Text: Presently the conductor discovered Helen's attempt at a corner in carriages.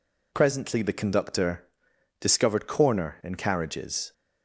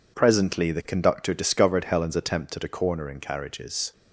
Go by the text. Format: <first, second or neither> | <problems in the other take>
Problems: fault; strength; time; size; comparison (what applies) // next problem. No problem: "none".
second | pauses between "conductor" and "discovered"; noticeable; at 1.6 s; 0.54 s long // skips "Helen's attempt at a"; at 2.6 s